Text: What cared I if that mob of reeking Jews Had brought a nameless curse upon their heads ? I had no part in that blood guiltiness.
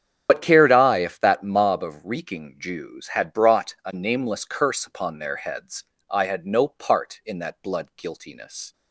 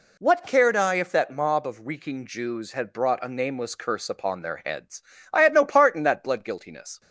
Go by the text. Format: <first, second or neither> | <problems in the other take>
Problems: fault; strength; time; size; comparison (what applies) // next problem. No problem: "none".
second | loses the start of "What"; at 0.2 s; 85 ms // starts louder than the rest; strong; until 1.3 s; 8.5 dB